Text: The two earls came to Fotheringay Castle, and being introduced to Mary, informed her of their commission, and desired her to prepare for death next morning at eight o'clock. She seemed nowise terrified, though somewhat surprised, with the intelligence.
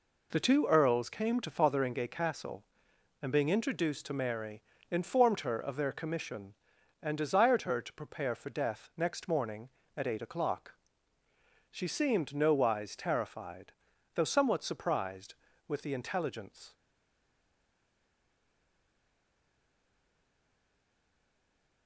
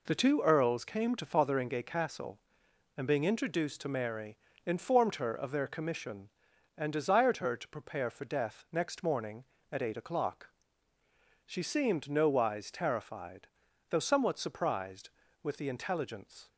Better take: second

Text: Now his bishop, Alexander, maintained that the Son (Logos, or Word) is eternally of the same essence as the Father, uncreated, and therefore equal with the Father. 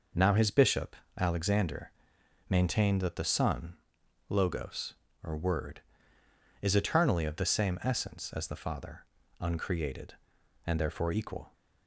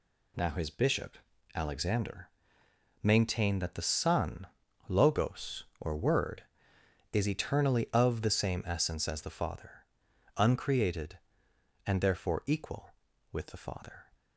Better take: second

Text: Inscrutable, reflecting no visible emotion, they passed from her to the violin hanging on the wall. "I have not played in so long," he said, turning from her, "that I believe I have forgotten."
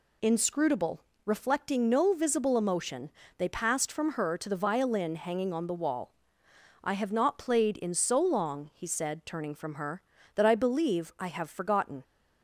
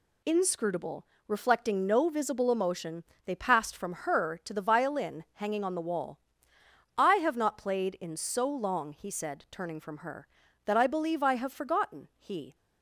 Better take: first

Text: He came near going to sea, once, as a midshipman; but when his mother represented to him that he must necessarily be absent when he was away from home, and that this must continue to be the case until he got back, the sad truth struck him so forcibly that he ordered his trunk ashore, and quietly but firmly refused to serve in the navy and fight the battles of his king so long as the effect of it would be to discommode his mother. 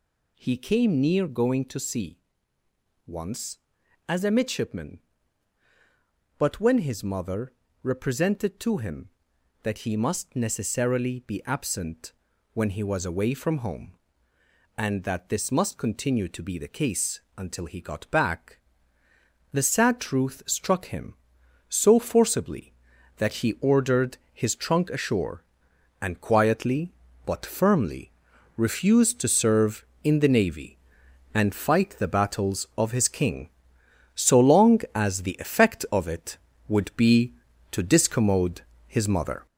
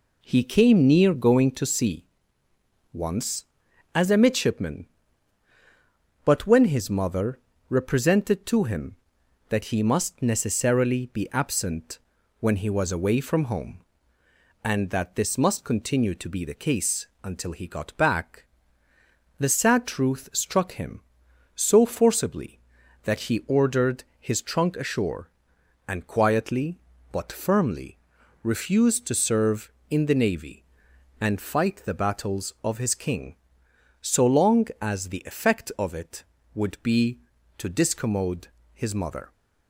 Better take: second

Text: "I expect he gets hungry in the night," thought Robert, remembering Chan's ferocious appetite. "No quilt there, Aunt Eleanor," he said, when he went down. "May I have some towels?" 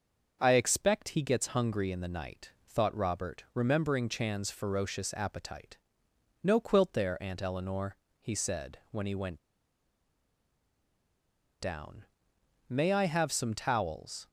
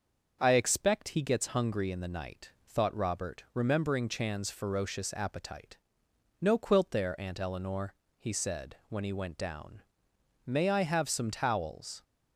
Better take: second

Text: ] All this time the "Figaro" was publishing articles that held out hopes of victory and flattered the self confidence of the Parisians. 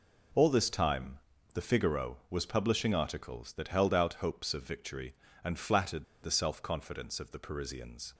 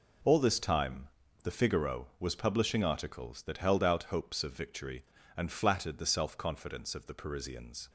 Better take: second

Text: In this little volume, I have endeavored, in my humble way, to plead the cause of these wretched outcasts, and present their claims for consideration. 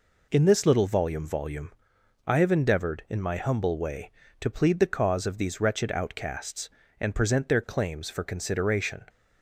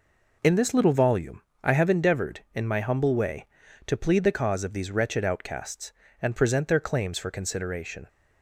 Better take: second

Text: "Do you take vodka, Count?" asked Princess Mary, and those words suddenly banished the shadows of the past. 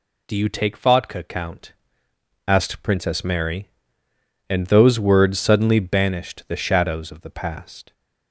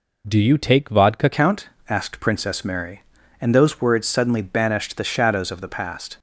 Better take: first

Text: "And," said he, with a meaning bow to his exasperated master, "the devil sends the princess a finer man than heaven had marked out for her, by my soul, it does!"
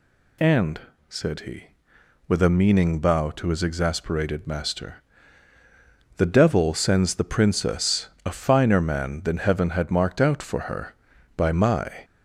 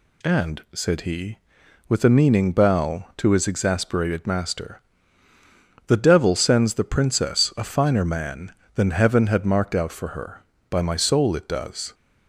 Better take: second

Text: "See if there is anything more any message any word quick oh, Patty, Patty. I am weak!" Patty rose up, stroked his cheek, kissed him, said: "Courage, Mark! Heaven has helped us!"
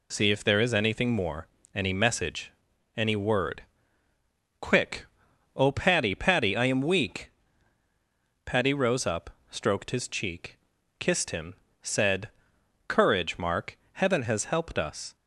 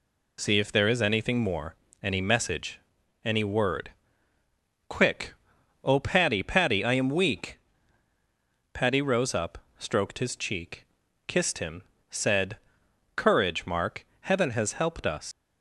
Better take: first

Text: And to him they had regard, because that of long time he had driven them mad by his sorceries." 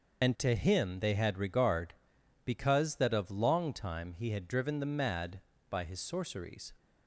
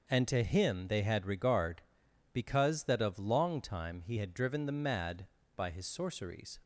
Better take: second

